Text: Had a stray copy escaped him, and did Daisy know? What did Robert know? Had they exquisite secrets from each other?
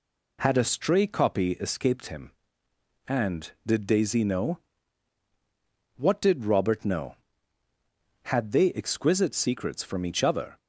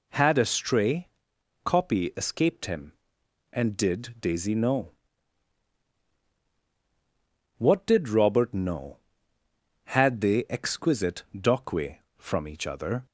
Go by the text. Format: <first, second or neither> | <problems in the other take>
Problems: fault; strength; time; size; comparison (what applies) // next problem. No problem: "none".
first | pauses between "stray" and "copy"; noticeable; at 1.0 s; 0.56 s long // says "dockway" for "secrets"; at 11.3 s